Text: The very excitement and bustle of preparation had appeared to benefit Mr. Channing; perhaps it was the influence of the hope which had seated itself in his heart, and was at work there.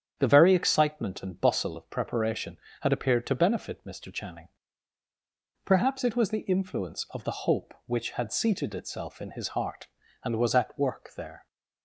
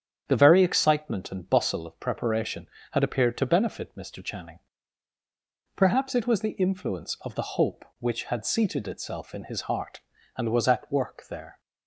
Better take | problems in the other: neither | starts louder than the rest; strong; the same in both

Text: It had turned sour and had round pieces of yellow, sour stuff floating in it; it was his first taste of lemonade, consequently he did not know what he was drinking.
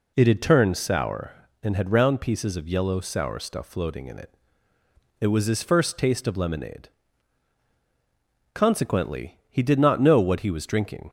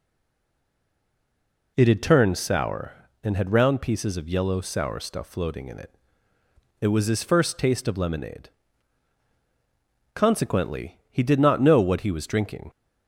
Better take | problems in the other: first | stays silent before the first word; noticeable; until 1.7 s; 1.7 s long

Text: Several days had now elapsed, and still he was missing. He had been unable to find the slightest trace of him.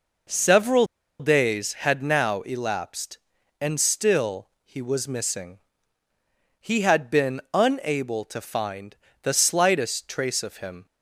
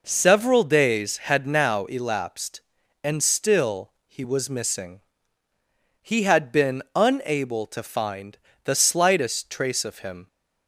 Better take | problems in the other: second | pauses between "Several" and "days"; slight; at 0.8 s; 0.35 s long // pauses between "find" and "the"; slight; at 8.9 s; 0.28 s long; slight in the second

